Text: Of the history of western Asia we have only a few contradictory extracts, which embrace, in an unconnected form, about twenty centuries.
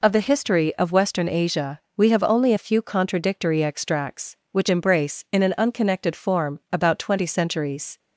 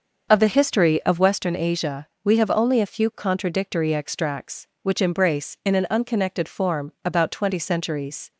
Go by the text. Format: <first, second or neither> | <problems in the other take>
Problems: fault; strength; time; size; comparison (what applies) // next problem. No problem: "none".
first | starts louder than the rest; noticeable; until 1.3 s; 6 dB // pauses between "Asia" and "we"; slight; at 2.0 s; 0.16 s long; slight in the first